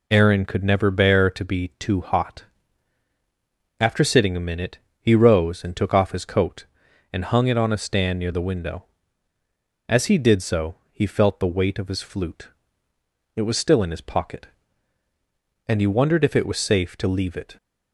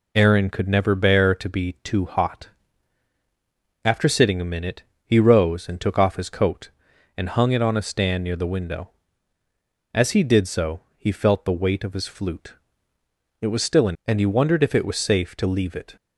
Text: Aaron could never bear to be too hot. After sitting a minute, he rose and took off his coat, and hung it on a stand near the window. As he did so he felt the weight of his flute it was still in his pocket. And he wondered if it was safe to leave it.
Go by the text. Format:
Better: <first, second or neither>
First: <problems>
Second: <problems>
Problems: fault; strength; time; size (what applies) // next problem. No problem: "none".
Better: first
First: pauses between "so" and "he"; slight; at 10.7 s; 0.16 s long // pauses between "flute" and "it"; noticeable; at 12.4 s; 0.86 s long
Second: pauses between "so" and "he"; slight; at 10.8 s; 0.16 s long // pauses between "flute" and "it"; noticeable; at 12.5 s; 0.86 s long // skips "his pocket"; at 14.0 s